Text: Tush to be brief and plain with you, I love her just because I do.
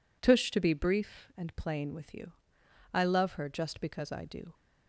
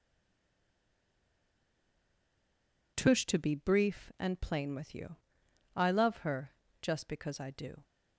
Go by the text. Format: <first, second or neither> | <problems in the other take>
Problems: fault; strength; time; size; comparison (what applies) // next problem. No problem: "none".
first | stays silent before the first word; strong; until 2.9 s; 2.9 s long // pauses between "her" and "just"; slight; at 6.5 s; 0.28 s long